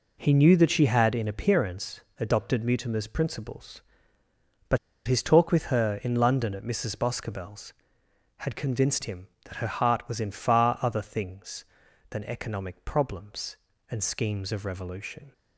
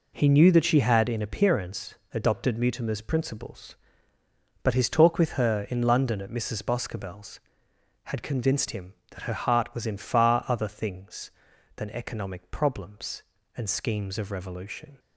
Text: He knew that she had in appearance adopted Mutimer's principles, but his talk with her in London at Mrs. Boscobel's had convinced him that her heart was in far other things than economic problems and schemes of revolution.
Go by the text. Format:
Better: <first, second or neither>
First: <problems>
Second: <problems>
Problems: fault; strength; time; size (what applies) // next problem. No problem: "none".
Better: second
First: pauses between "appearance" and "adopted"; slight; at 2.0 s; 0.18 s long // pauses between "but" and "his"; slight; at 4.7 s; 0.30 s long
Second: pauses between "appearance" and "adopted"; slight; at 1.9 s; 0.18 s long